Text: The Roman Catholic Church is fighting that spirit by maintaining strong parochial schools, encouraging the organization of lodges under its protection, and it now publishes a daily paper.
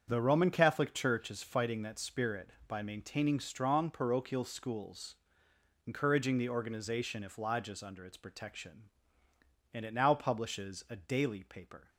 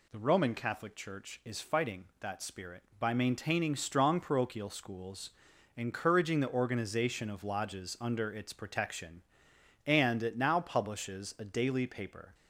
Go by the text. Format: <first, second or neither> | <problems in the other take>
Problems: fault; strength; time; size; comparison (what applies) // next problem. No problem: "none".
second | starts louder than the rest; strong; until 1.0 s; 7.5 dB // says "if" for "of"; at 7.2 s